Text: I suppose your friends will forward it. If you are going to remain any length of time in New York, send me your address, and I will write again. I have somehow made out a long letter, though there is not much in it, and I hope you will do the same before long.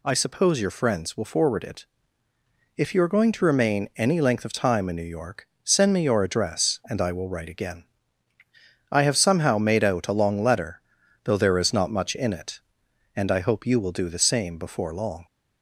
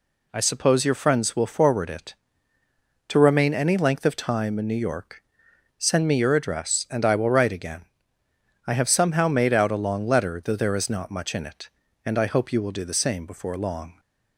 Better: first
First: none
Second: skips "If you are going"; at 2.6 s

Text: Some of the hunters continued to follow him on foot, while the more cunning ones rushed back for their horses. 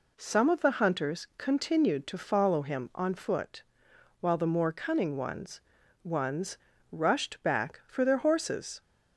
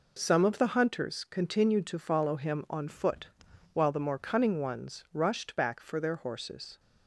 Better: second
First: says "ones" twice; at 6.0 s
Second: none

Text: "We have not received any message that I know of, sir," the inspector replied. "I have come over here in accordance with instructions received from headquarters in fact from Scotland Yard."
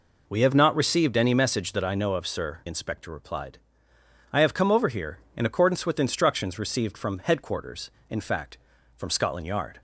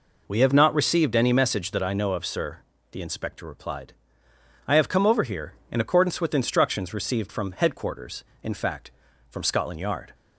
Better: second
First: skips "the"; at 2.6 s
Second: none

